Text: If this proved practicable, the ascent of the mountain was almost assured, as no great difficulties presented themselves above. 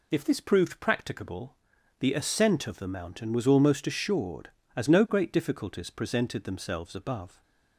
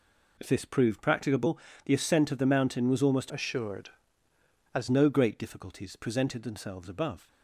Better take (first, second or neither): first